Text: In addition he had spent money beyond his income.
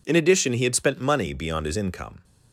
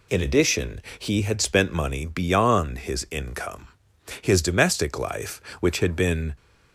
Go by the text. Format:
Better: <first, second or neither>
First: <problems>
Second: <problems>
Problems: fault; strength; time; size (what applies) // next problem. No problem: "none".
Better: first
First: none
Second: pauses between "addition" and "he"; slight; at 0.8 s; 0.16 s long // goes on to say "His domestic life which had been"; strong; from 4.2 s on; 2.1 s long